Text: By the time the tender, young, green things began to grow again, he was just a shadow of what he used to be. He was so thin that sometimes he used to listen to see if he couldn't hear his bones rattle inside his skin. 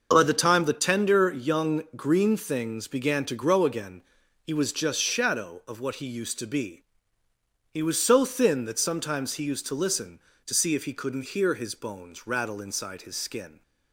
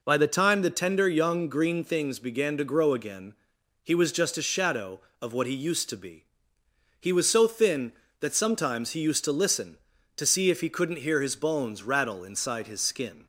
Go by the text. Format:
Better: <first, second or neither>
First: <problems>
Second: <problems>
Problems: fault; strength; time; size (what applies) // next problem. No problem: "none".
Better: second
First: starts louder than the rest; until 1.1 s; 6 dB // skips "a"; at 4.9 s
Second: none